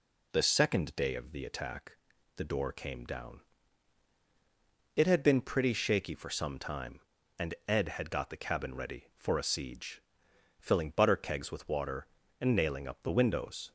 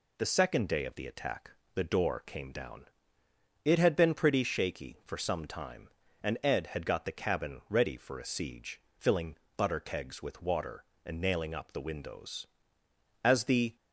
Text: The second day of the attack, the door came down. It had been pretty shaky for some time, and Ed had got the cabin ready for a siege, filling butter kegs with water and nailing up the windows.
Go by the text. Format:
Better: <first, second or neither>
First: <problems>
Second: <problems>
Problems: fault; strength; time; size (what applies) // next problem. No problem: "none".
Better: first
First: none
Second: pauses between "filling" and "butter"; slight; at 9.3 s; 0.20 s long // goes on to say "As the"; from 13.2 s on; 0.52 s long